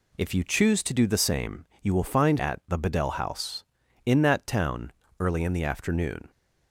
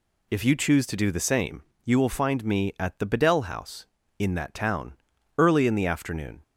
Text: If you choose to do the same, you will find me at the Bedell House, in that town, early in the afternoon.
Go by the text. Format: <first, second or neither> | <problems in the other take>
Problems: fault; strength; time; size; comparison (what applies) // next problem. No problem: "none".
second | skips "me"; at 2.3 s